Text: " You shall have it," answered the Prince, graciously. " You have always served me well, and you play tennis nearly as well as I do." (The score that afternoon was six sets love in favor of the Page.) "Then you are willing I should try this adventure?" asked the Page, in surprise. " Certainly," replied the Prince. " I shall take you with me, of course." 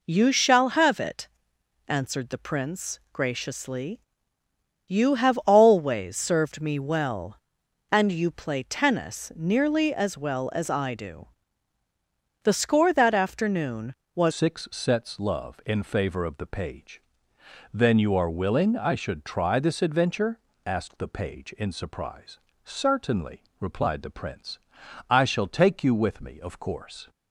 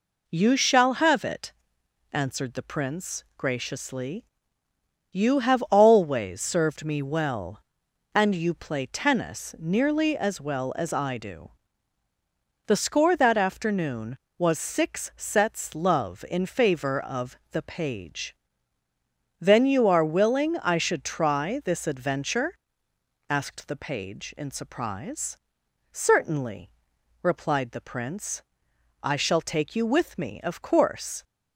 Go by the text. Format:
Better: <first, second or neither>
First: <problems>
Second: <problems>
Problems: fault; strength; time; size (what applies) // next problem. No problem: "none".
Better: second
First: changes voice at "six"; from 14.3 s on; 12.7 s long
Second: none